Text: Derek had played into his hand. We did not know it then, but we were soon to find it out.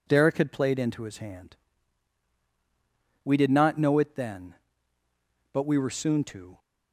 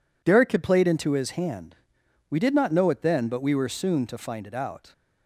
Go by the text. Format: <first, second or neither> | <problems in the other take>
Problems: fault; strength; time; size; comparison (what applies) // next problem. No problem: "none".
second | stops before "find it out"; at 6.5 s